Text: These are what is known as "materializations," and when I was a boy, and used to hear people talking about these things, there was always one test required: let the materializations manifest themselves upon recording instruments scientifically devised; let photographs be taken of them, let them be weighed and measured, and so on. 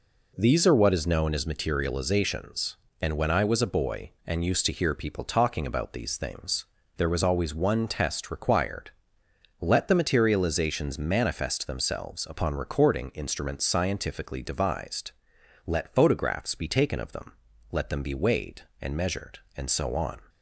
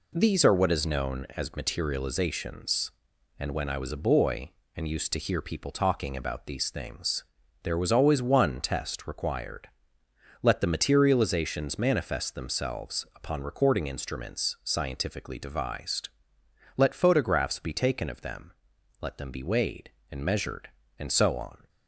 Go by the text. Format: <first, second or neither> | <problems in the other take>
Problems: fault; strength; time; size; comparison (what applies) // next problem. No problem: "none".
neither | none